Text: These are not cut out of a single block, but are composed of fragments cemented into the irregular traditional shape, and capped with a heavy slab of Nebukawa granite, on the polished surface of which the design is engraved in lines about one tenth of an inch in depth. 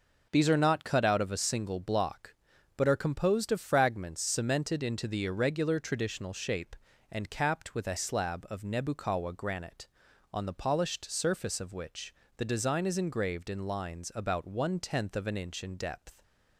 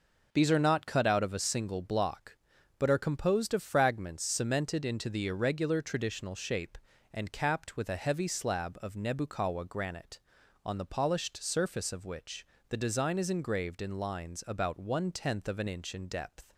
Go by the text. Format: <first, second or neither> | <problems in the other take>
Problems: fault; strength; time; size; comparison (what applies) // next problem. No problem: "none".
second | skips "heavy"; at 7.9 s // pauses between "which" and "the"; slight; at 12.1 s; 0.22 s long; slight in the second